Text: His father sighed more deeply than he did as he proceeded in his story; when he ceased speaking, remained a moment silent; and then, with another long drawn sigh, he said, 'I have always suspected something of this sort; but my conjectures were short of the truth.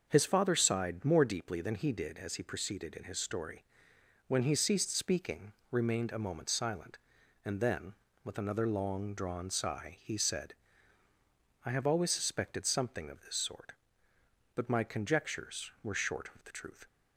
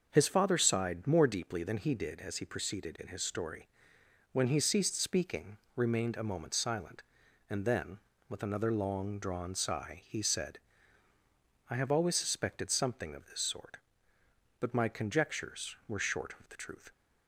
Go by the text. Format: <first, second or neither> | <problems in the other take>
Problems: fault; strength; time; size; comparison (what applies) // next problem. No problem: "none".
neither | starts louder than the rest; the same in both